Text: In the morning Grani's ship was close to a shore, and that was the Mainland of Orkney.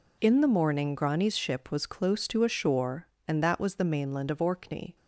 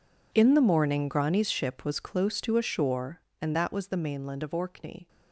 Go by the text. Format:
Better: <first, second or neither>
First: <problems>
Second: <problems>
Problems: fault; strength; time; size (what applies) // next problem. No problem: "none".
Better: first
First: none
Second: gets quieter; strong; throughout; 18.5 dB